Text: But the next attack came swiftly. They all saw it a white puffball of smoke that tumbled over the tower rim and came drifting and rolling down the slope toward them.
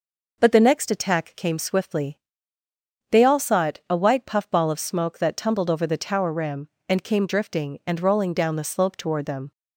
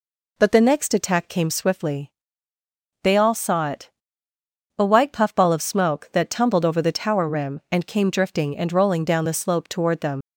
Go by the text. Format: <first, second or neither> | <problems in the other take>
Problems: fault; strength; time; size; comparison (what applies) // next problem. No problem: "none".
first | pauses between "it" and "a"; noticeable; at 3.9 s; 0.88 s long // leaves "them" unfinished; at 10.2 s; 70 ms